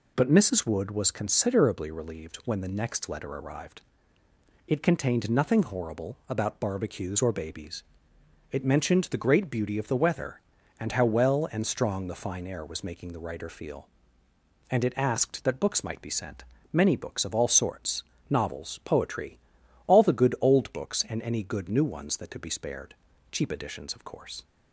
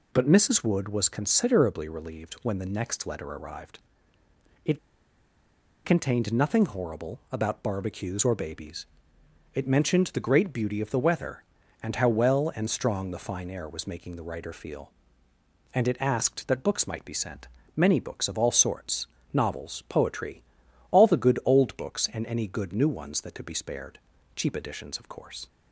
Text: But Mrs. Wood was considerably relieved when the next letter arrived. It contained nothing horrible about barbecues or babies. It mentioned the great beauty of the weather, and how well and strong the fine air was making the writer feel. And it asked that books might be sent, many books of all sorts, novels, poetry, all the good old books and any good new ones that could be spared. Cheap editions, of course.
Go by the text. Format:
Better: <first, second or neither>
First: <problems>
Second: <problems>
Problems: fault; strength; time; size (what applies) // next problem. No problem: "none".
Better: first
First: none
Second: pauses between "It" and "contained"; at 4.7 s; 1.0 s long